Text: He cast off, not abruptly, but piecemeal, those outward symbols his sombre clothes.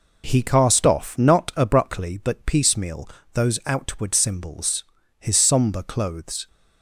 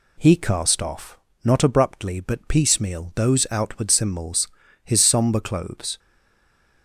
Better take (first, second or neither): first